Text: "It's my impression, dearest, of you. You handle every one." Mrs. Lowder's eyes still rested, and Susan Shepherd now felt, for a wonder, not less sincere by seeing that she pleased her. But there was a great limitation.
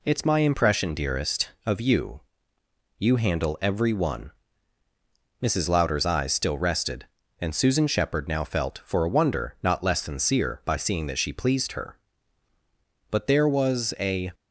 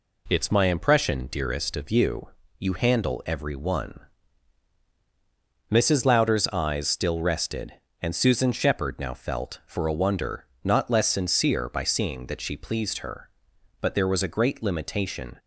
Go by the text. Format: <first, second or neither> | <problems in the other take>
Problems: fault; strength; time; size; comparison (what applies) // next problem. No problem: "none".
second | stops before "great limitation"; at 14.3 s